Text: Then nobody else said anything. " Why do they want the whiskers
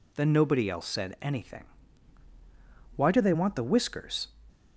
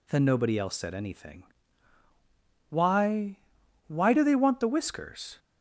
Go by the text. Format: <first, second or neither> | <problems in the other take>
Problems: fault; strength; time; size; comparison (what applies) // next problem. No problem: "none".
first | says "Why" twice; at 3.8 s